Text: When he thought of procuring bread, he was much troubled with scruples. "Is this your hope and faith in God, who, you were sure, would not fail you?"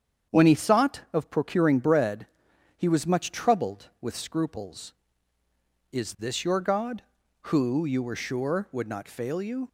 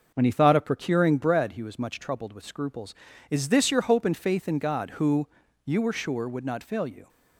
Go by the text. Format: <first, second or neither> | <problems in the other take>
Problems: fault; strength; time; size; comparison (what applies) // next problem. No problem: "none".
second | starts louder than the rest; strong; until 1.4 s; 8 dB // skips "hope and faith in"; at 6.6 s